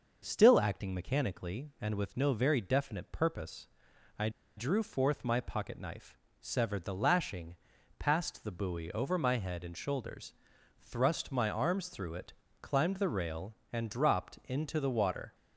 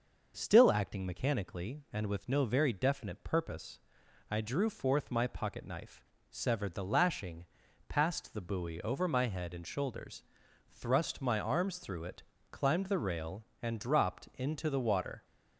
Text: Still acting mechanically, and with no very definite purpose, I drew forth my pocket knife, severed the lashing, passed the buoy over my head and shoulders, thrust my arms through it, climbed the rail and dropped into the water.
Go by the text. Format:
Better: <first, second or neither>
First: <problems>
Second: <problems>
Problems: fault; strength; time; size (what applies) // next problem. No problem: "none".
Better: second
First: pauses between "I" and "drew"; slight; at 4.2 s; 0.27 s long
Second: none